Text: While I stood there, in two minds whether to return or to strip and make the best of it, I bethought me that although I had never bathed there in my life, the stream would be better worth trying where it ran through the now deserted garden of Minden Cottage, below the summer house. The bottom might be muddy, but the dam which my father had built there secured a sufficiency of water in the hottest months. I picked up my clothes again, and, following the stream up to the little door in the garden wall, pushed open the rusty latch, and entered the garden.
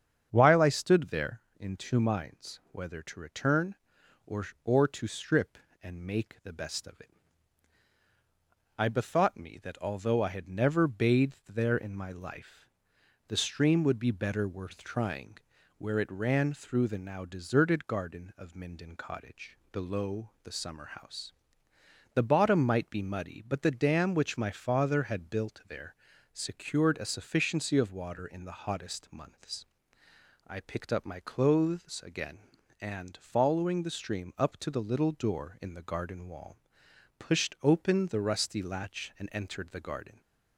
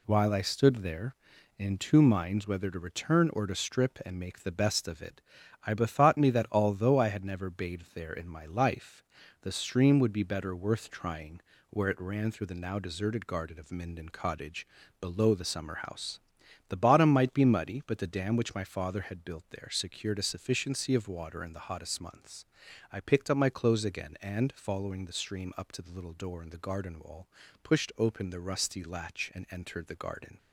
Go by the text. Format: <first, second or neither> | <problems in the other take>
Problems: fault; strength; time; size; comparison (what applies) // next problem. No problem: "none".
second | starts louder than the rest; strong; until 1.3 s; 7.5 dB // says "or" twice; at 4.6 s // pauses between "trying" and "where"; at 15.3 s; 0.40 s long; slight in the second // pauses between "there" and "secured"; slight; at 25.9 s; 0.36 s long